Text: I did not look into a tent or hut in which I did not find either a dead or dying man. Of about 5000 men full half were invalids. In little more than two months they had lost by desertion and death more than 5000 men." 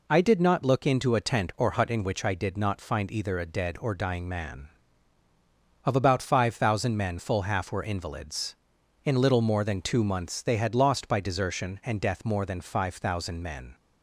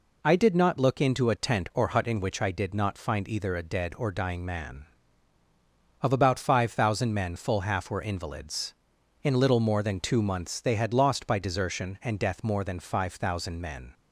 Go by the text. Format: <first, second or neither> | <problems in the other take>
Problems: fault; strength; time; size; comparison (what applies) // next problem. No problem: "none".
neither | none